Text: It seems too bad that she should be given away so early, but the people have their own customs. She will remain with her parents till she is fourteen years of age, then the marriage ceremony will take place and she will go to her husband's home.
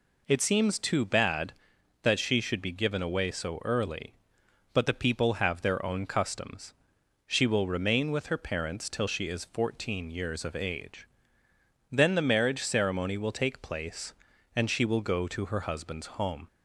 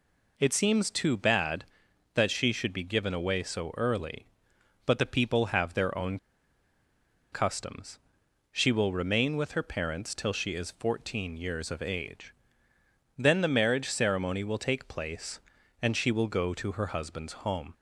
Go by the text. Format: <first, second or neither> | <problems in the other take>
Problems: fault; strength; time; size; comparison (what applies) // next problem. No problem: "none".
first | pauses between "own" and "customs"; at 6.1 s; 1.1 s long